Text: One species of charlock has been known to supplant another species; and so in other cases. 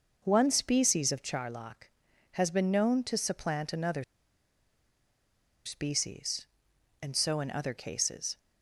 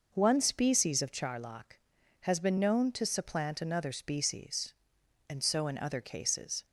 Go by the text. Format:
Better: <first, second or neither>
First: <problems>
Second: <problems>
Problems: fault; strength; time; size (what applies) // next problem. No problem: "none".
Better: second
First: pauses between "another" and "species"; strong; at 4.0 s; 1.6 s long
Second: none